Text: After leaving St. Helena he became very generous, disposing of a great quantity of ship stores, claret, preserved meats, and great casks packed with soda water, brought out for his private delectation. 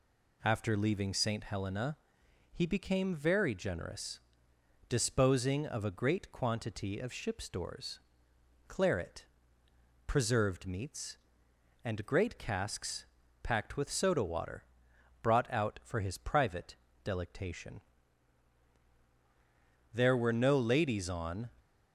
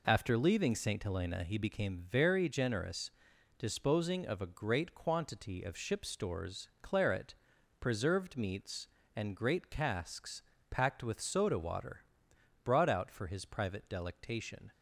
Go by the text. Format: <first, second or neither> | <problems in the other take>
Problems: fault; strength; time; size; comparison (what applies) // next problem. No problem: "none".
second | pauses between "Helena" and "he"; noticeable; at 1.9 s; 0.56 s long // pauses between "casks" and "packed"; slight; at 13.0 s; 0.36 s long; slight in the second // pauses between "private" and "delectation"; slight; at 16.7 s; 0.28 s long // goes on to say "There were no ladies on"; from 19.9 s on; 1.5 s long